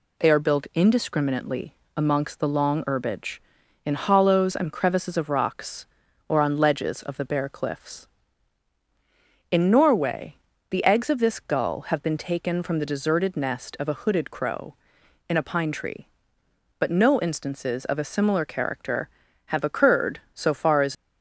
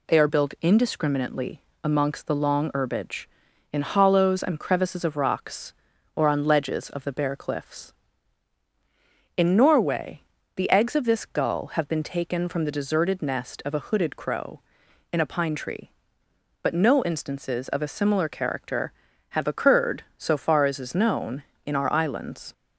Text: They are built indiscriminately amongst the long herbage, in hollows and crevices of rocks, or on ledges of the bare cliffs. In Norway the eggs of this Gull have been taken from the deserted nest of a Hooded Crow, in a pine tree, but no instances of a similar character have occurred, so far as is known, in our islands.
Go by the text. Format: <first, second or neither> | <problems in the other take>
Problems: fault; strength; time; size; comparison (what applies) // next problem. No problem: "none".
second | pauses between "indiscriminately" and "amongst"; slight; at 1.7 s; 0.18 s long; slight in the second // pauses between "Norway" and "the"; slight; at 10.3 s; 0.32 s long; slight in the second // stops before "is known in our islands"; at 20.9 s